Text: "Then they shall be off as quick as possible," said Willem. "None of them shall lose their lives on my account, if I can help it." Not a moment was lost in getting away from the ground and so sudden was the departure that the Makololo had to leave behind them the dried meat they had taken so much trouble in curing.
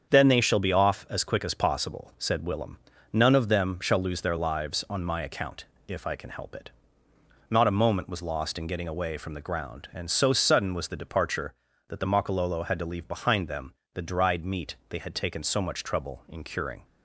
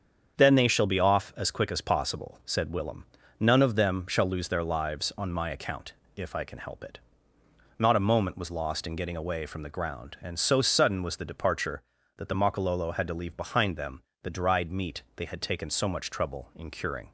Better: neither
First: starts louder than the rest; strong; until 1.1 s; 7.5 dB // pauses between "them" and "the"; slight; at 13.7 s; 0.22 s long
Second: starts louder than the rest; strong; until 1.4 s; 7.5 dB // pauses between "them" and "the"; slight; at 14.0 s; 0.22 s long

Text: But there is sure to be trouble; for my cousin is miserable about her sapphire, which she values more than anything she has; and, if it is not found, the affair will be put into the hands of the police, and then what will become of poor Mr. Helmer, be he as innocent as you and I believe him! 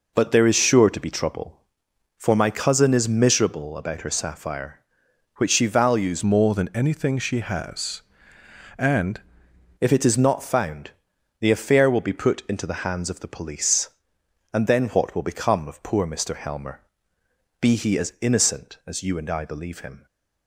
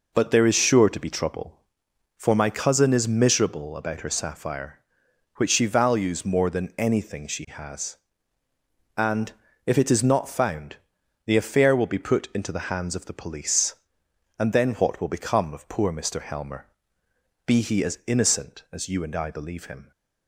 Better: second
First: changes voice from "more" to "and"; from 6.2 to 9.2 s; 3.0 s long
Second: none

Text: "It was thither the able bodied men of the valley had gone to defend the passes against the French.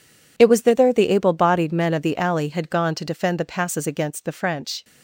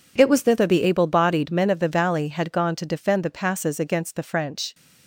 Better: second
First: says "alley" for "valley"; at 2.1 s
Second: none

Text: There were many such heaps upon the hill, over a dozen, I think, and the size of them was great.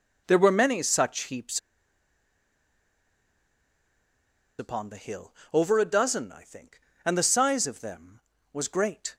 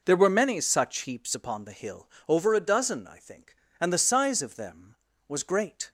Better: second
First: pauses between "heaps" and "upon"; strong; at 1.5 s; 2.9 s long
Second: none

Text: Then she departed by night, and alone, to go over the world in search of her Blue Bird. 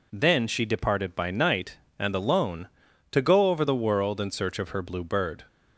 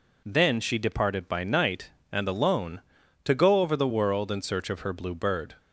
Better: neither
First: none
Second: none

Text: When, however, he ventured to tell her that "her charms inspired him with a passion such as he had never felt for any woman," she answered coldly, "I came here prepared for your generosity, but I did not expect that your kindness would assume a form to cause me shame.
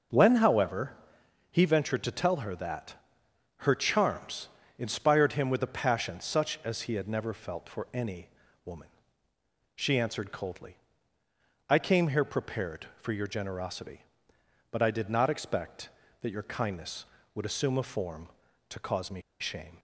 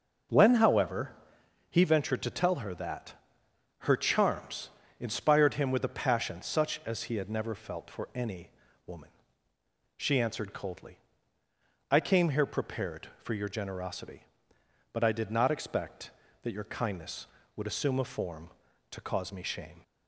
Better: second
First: pauses between "that" and "her"; noticeable; at 2.9 s; 0.64 s long // pauses between "charms" and "inspired"; slight; at 4.4 s; 0.28 s long // pauses between "any" and "woman"; at 8.2 s; 0.38 s long // pauses between "me" and "shame"; slight; at 19.2 s; 0.19 s long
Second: pauses between "that" and "her"; noticeable; at 3.1 s; 0.66 s long // pauses between "charms" and "inspired"; slight; at 4.7 s; 0.28 s long // pauses between "any" and "woman"; at 8.4 s; 0.38 s long

